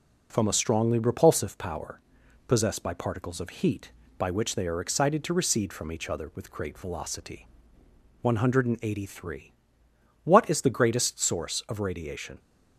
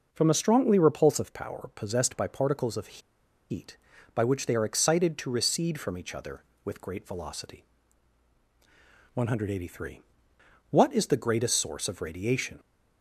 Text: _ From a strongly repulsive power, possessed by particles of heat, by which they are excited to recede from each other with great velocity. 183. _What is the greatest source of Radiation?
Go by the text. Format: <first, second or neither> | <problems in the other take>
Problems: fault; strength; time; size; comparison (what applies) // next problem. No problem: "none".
first | pauses between "of" and "heat"; noticeable; at 2.9 s; 0.51 s long